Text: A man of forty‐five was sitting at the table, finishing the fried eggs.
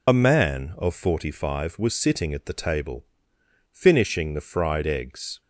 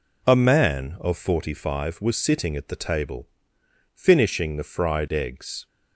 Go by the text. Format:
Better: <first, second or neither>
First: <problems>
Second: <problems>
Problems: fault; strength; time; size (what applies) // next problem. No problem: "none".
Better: second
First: loses the start of "A"; at 0.0 s; 55 ms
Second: none